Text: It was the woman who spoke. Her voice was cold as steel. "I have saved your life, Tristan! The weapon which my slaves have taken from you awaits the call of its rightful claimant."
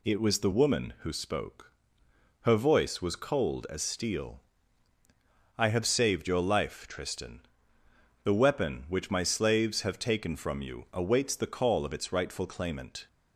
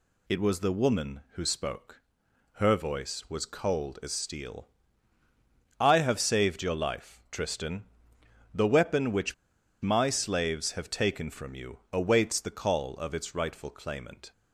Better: first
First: none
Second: pauses between "which" and "my"; noticeable; at 9.3 s; 0.49 s long

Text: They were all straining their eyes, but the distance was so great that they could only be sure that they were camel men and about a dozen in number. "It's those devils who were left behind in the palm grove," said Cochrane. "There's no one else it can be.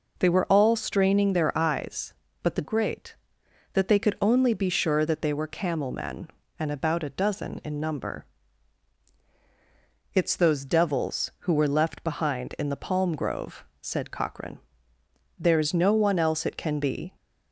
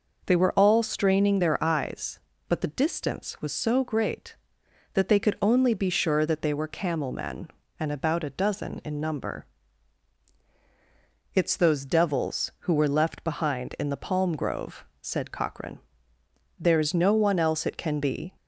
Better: second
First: skips "distance was so"; at 2.6 s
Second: none

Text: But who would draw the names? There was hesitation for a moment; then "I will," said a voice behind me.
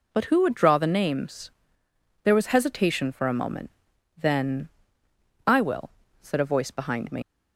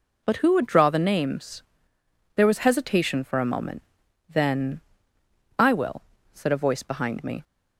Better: second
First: pauses between "then" and "I"; noticeable; at 4.6 s; 0.80 s long // leaves "me" unfinished; at 7.2 s; 85 ms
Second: pauses between "then" and "I"; noticeable; at 4.7 s; 0.80 s long

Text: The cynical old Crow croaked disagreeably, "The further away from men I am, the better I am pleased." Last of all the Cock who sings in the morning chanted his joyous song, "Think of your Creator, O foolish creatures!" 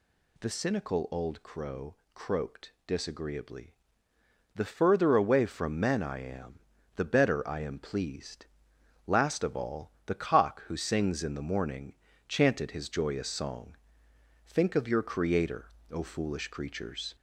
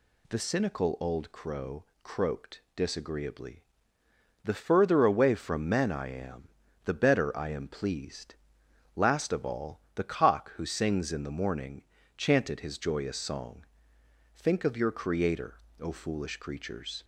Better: second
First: gets louder; slight; throughout; 2 dB // pauses between "Crow" and "croaked"; slight; at 1.9 s; 0.18 s long // pauses between "morning" and "chanted"; slight; at 11.9 s; 0.34 s long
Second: pauses between "Crow" and "croaked"; slight; at 1.8 s; 0.18 s long // pauses between "morning" and "chanted"; slight; at 11.8 s; 0.34 s long

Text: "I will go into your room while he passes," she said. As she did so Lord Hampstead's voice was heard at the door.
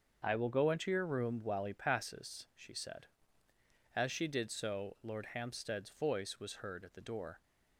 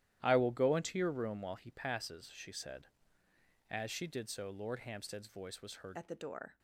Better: first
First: starts louder than the rest; until 1.2 s; 6.5 dB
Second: starts louder than the rest; strong; until 1.2 s; 12.5 dB // changes voice at "at"; from 5.9 s on; 0.6 s long

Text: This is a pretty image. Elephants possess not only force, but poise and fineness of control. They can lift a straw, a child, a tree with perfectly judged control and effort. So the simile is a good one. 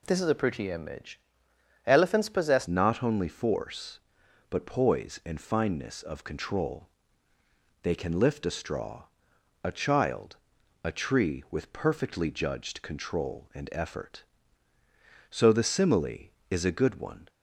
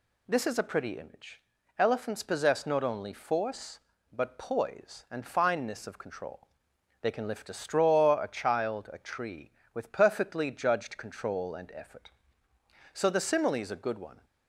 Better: second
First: changes voice at "not"; from 2.6 s on; 14.6 s long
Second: none

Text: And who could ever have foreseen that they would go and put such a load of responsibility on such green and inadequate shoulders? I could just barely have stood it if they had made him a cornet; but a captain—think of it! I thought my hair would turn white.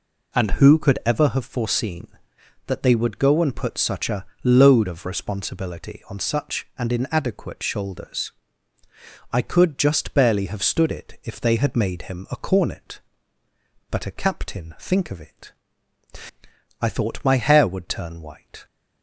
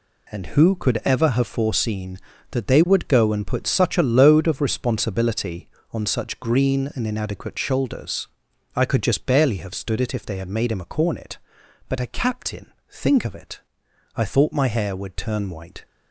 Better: second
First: pauses between "a" and "load"; slight; at 4.2 s; 0.18 s long // skips "green"; at 6.7 s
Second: none

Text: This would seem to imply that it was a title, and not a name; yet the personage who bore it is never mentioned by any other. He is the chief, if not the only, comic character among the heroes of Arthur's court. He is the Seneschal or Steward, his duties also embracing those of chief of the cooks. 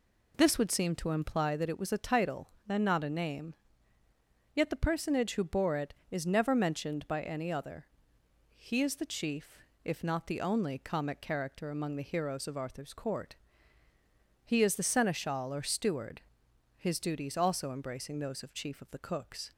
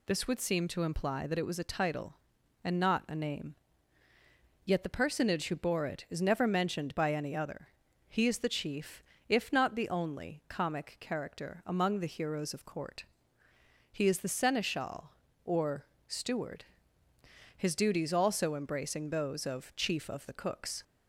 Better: first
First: none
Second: skips "Arthur's"; at 12.6 s // pauses between "or" and "Steward"; slight; at 15.8 s; 0.22 s long

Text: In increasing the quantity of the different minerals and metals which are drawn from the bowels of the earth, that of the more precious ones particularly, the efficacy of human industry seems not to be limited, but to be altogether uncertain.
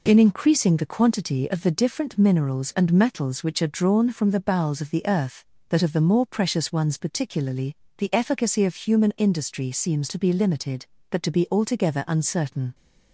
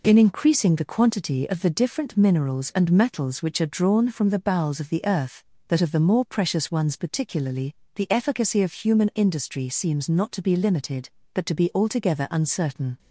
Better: second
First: skips "not"; at 10.0 s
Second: none

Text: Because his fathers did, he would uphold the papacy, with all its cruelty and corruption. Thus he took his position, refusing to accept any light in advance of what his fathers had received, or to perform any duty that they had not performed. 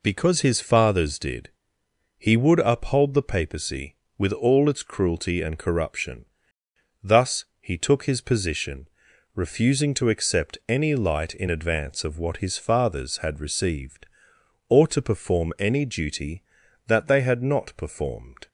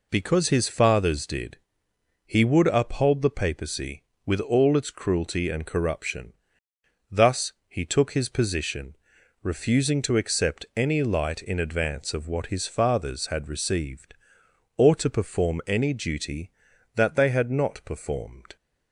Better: neither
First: none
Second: none

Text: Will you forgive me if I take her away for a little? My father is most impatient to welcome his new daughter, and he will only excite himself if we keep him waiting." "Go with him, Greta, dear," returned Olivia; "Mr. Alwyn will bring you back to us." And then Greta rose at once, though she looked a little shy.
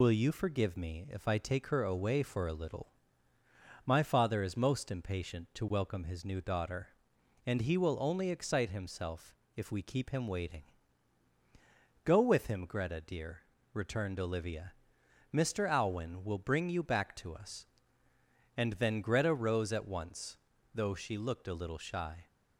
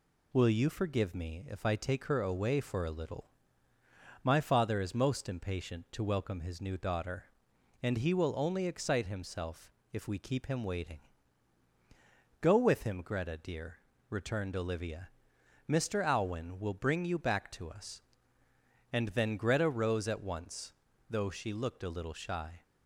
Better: second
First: loses the start of "Will"; at 0.0 s; 45 ms // pauses between "himself" and "if"; slight; at 9.3 s; 0.22 s long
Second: pauses between "himself" and "if"; slight; at 9.7 s; 0.22 s long

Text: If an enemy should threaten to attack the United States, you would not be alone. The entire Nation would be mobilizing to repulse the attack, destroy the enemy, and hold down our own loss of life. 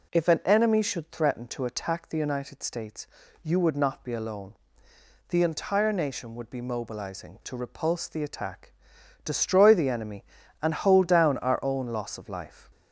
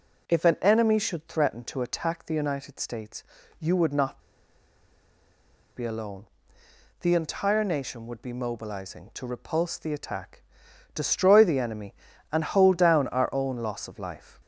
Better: first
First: none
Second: pauses between "not" and "be"; strong; at 4.1 s; 1.5 s long

